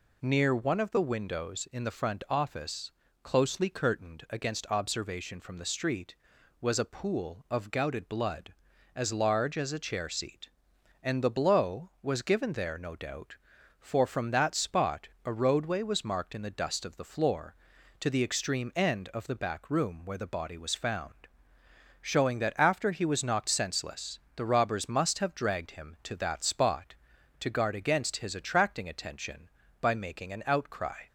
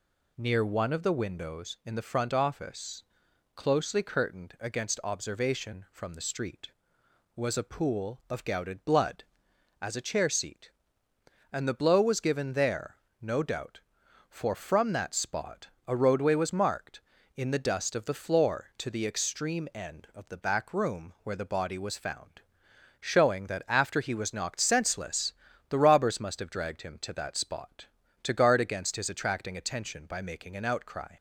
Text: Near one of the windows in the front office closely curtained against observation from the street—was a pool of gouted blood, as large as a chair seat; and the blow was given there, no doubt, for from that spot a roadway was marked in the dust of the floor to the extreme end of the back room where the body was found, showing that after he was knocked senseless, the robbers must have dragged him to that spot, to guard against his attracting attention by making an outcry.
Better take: first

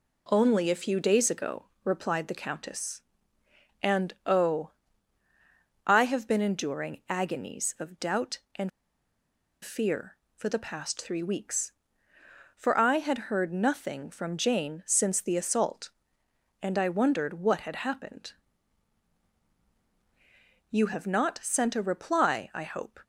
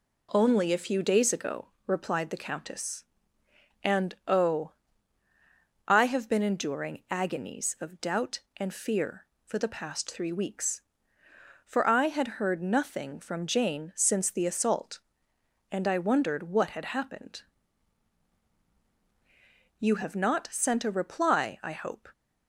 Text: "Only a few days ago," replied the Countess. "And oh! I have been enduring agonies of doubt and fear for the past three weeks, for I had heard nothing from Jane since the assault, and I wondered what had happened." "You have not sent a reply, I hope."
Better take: second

